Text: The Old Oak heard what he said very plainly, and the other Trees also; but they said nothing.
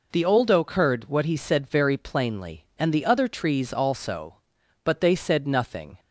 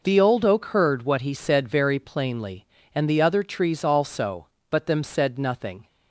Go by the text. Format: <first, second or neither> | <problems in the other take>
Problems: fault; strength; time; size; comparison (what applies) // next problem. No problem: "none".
first | says "them" for "they"; at 4.8 s